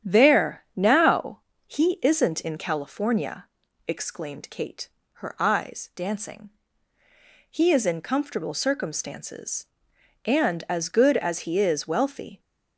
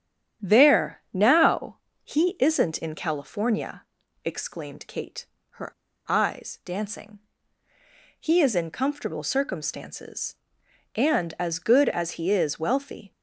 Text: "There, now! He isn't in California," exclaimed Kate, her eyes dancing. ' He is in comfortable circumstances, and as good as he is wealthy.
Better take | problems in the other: first | starts louder than the rest; strong; until 1.5 s; 10.5 dB; strong in the first // pauses between "her" and "eyes"; slight; at 5.7 s; 0.36 s long

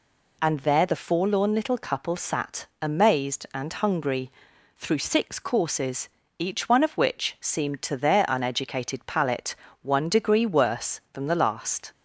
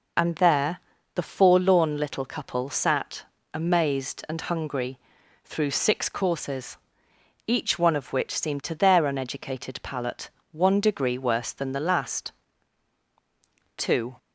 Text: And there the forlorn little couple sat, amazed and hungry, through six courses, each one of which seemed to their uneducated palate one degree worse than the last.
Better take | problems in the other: first | pauses between "there" and "the"; slight; at 0.7 s; 0.34 s long // pauses between "palate" and "one"; slight; at 10.2 s; 0.22 s long; slight in the first // goes on to say "Two"; slight; from 13.7 s on; 0.40 s long

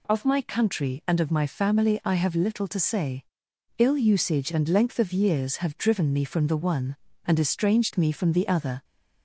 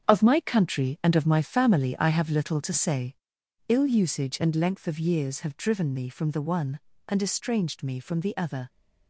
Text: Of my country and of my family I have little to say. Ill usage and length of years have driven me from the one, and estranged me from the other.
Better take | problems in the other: first | gets quieter; strong; throughout; 8.5 dB

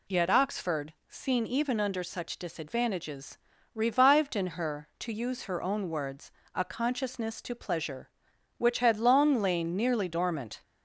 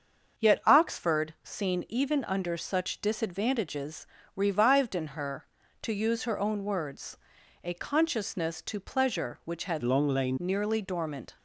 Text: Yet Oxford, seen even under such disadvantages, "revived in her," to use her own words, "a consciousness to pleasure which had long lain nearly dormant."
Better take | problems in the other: first | starts louder than the rest; until 1.5 s; 6.5 dB // changes voice from "long" to "lain"; from 9.8 to 10.3 s; 0.5 s long

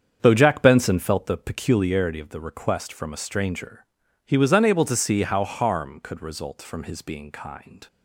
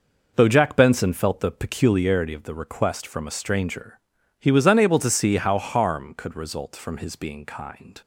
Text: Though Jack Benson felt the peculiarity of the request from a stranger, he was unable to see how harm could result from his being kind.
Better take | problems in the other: second | starts louder than the rest; strong; until 1.3 s; 7.5 dB

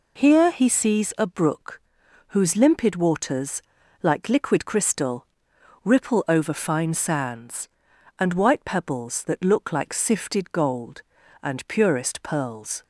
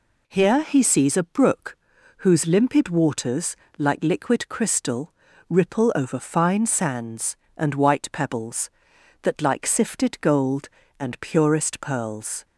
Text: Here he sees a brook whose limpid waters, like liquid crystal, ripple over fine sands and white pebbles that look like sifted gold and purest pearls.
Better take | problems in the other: first | pauses between "brook" and "whose"; at 1.7 s; 0.42 s long; noticeable in the first // skips "look"; at 9.4 s

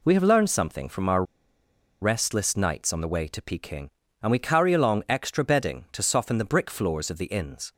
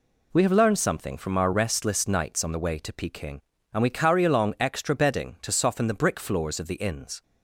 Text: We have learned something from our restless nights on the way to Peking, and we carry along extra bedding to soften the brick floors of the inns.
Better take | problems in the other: second | pauses between "our" and "restless"; noticeable; at 1.2 s; 0.78 s long

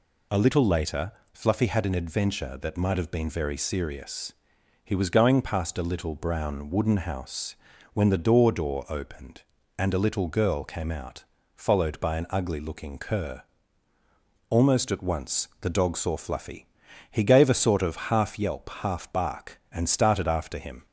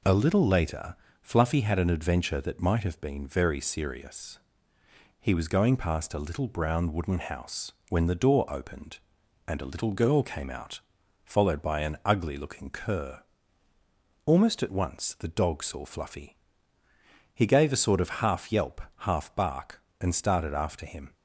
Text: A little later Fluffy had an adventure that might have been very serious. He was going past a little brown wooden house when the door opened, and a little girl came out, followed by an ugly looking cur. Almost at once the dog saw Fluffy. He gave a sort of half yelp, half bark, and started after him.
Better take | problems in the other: second | pauses between "later" and "Fluffy"; slight; at 1.1 s; 0.22 s long; slight in the second // pauses between "house" and "when"; at 7.5 s; 0.38 s long; slight in the second // says "door" twice; at 8.5 s

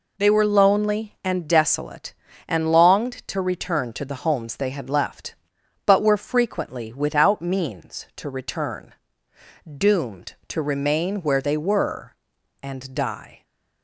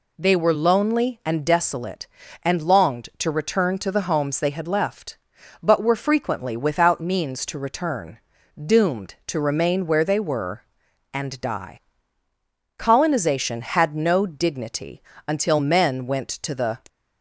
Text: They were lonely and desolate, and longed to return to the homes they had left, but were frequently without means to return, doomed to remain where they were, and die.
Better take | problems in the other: first | goes on to say "Colonization had no dignity until men went to the"; strong; from 12.7 s on; 4.0 s long

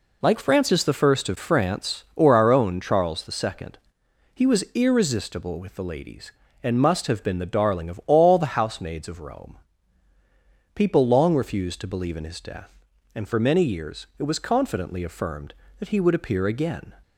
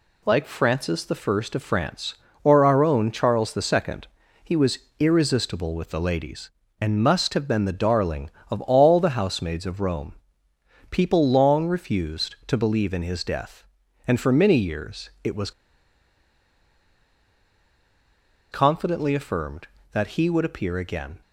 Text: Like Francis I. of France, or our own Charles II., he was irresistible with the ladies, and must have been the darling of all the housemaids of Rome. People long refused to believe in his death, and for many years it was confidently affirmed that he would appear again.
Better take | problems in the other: first | pauses between "was" and "irresistible"; slight; at 4.7 s; 0.22 s long // pauses between "was" and "confidently"; strong; at 15.5 s; 3.0 s long

